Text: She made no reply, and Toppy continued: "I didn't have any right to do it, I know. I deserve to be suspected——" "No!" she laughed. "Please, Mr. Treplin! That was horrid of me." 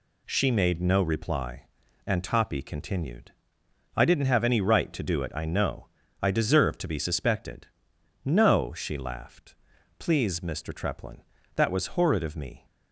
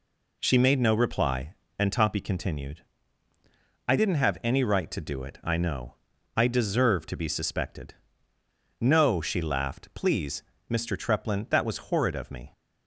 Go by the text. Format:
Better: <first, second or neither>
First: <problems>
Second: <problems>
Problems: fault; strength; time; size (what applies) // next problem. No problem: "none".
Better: neither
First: none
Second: none